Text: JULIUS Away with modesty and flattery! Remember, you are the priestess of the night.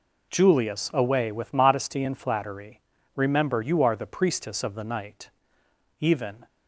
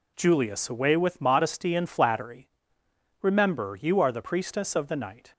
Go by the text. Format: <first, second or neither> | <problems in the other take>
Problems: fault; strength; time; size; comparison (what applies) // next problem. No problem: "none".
second | goes on to say "Even"; slight; from 5.9 s on; 0.46 s long